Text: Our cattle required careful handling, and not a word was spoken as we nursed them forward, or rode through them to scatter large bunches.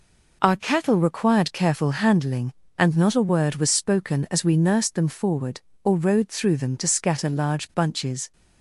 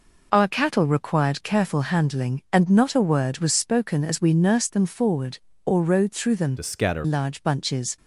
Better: first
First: none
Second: changes voice from "to" to "scatter"; from 6.5 to 7.0 s; 0.5 s long

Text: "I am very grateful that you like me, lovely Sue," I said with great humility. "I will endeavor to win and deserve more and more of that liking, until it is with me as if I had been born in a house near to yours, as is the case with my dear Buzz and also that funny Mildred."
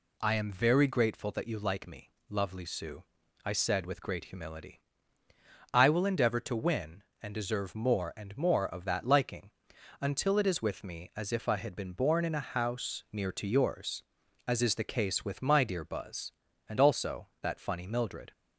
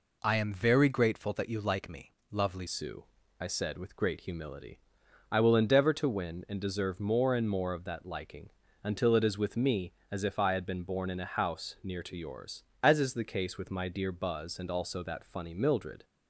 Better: first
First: none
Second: changes voice at "Sue"; from 2.6 s on; 13.4 s long

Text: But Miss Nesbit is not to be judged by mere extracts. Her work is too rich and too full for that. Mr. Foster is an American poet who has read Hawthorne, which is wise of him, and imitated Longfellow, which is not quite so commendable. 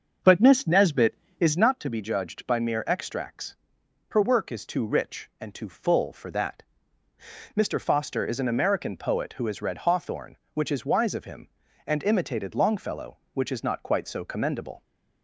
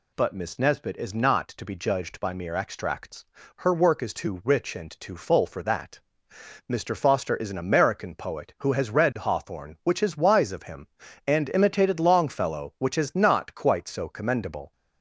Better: second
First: starts louder than the rest; until 1.7 s; 6.5 dB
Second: none

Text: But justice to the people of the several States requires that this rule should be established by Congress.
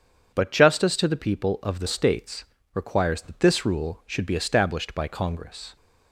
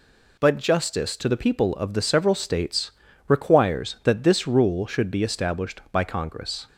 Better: second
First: starts louder than the rest; strong; until 1.3 s; 7 dB // skips "several"; at 1.8 s // pauses between "States" and "requires"; slight; at 2.4 s; 0.28 s long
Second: pauses between "States" and "requires"; at 2.9 s; 0.38 s long

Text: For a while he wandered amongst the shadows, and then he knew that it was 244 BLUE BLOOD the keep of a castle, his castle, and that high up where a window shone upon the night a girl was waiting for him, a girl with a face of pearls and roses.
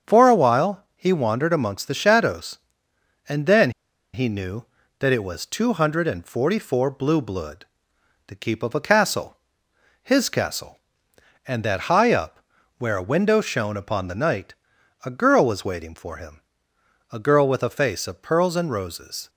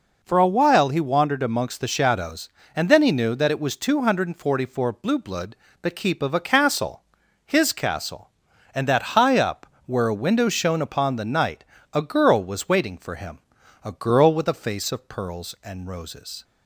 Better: second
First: starts louder than the rest; strong; until 1.1 s; 7.5 dB // pauses between "then" and "he"; at 3.7 s; 0.43 s long // pauses between "BLOOD" and "the"; noticeable; at 7.6 s; 0.62 s long // pauses between "up" and "where"; at 12.3 s; 0.38 s long // pauses between "night" and "a"; noticeable; at 14.5 s; 0.50 s long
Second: pauses between "BLOOD" and "the"; slight; at 5.5 s; 0.26 s long // pauses between "up" and "where"; slight; at 9.6 s; 0.20 s long // pauses between "night" and "a"; slight; at 11.6 s; 0.28 s long

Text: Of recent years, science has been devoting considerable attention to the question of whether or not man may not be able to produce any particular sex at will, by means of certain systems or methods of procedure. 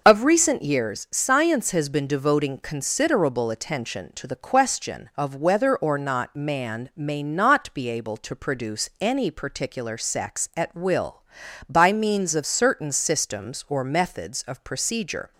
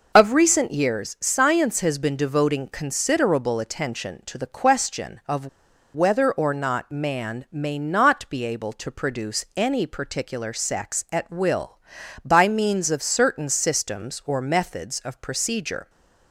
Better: first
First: none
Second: pauses between "of" and "whether"; noticeable; at 5.4 s; 0.47 s long

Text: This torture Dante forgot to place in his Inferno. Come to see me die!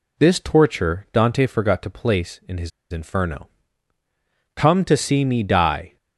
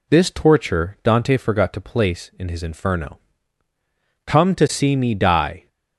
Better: second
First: pauses between "his" and "Inferno"; slight; at 2.7 s; 0.22 s long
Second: none

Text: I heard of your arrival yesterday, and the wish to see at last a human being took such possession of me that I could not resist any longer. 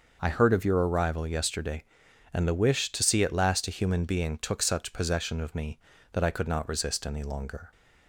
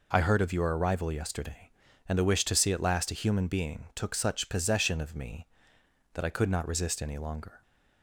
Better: neither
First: none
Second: none

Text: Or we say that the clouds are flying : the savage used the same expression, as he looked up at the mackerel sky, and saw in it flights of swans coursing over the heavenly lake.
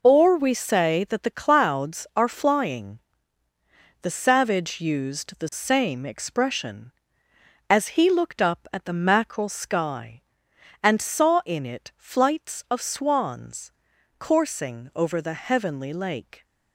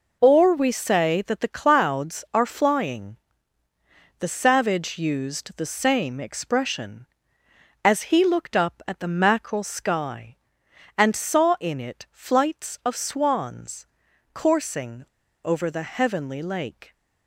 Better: first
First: pauses between "swans" and "coursing"; noticeable; at 13.7 s; 0.48 s long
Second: pauses between "swans" and "coursing"; noticeable; at 13.8 s; 0.48 s long // pauses between "coursing" and "over"; at 15.0 s; 0.39 s long

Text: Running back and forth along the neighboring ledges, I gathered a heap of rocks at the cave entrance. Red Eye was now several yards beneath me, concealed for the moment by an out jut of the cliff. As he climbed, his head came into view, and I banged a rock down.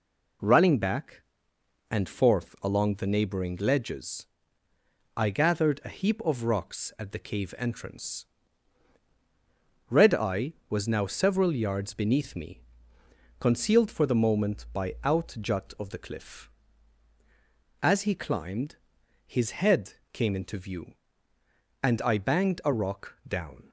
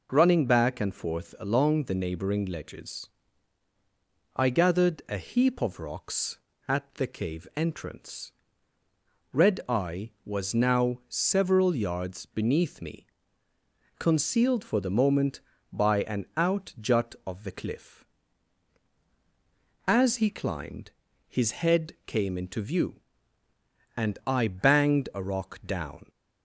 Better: second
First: skips "an"; at 14.9 s // pauses between "head" and "came"; slight; at 19.9 s; 0.18 s long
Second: none

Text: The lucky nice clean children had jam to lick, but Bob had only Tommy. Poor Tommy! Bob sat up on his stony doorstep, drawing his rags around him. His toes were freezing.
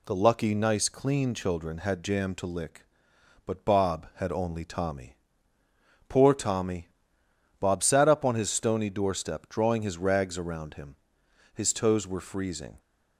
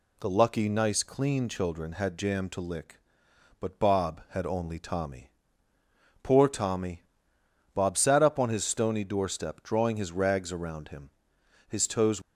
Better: first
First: none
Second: stops before "were freezing"; at 12.2 s

